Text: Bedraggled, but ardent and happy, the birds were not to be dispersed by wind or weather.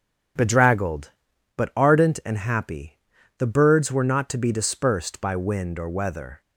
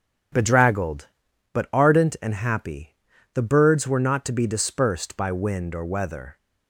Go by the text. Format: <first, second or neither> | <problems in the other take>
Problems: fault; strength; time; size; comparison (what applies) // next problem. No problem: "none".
neither | starts louder than the rest; strong; the same in both